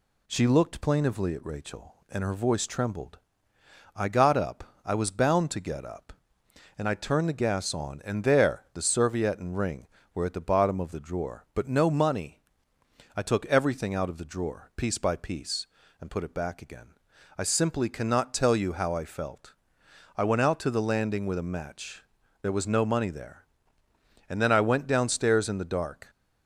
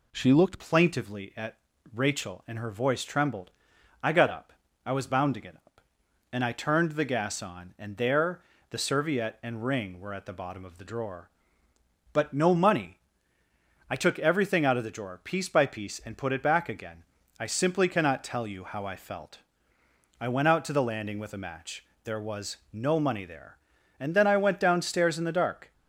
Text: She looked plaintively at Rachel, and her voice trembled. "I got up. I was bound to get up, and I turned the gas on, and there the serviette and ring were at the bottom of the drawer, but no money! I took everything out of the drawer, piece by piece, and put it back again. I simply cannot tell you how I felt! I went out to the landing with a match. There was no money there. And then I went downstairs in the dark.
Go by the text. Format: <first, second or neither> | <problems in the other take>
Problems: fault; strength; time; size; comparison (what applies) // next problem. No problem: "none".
first | changes voice at "plaintively"; from 0.5 s on; 25.2 s long // pauses between "at" and "Rachel"; slight; at 1.5 s; 0.36 s long // pauses between "there" and "the"; slight; at 8.4 s; 0.30 s long // pauses between "was" and "no"; slight; at 22.5 s; 0.16 s long